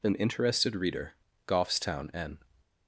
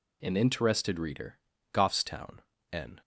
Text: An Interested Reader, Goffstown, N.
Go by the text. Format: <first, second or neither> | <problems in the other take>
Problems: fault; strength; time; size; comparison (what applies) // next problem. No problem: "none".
neither | none